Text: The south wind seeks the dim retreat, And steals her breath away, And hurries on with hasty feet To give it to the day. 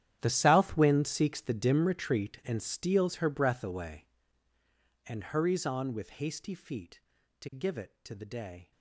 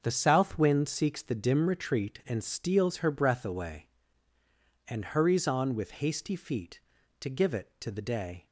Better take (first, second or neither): second